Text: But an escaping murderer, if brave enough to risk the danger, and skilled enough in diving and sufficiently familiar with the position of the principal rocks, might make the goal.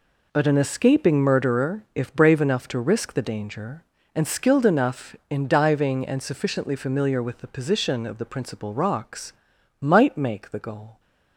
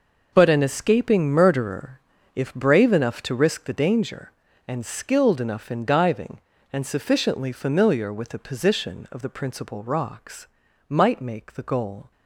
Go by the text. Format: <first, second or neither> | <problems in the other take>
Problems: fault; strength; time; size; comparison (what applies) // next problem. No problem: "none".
neither | none